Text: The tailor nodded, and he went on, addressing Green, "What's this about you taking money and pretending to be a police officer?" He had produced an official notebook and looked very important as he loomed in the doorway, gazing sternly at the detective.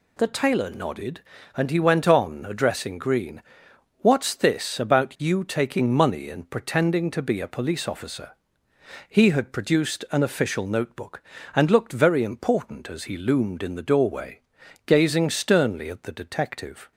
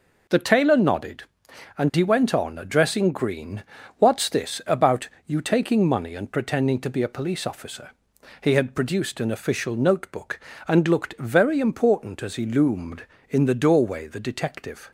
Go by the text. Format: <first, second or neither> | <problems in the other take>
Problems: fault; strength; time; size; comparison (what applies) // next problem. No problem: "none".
first | pauses between "about" and "you"; slight; at 5.0 s; 0.16 s long // skips "gazing sternly at"; at 14.0 s